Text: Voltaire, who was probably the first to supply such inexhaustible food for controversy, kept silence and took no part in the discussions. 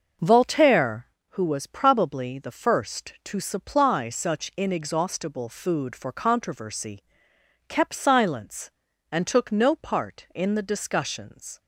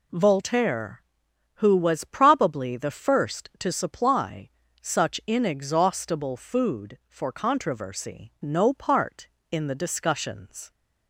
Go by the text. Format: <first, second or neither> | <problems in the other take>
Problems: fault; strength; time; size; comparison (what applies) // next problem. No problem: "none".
first | pauses between "supply" and "such"; slight; at 4.4 s; 0.34 s long // skips "kept silence and took"; at 8.3 s